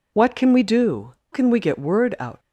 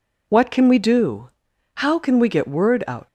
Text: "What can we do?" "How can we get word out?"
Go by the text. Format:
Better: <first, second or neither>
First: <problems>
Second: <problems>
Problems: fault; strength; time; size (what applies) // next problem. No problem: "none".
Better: second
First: skips "How"; at 1.2 s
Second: none